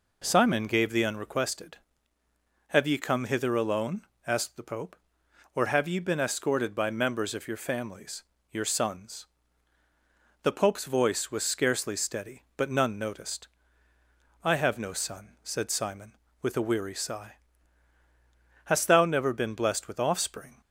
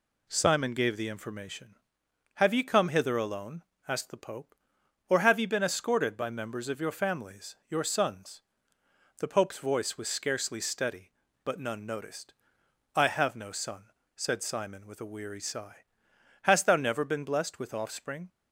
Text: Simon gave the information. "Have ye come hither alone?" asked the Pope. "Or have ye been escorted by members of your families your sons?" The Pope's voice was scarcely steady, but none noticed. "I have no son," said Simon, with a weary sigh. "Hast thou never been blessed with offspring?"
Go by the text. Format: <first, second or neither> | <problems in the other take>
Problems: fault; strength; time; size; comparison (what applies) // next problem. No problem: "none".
second | says "unrequested" for "information"; at 1.0 s // pauses between "families" and "your"; slight; at 8.2 s; 0.30 s long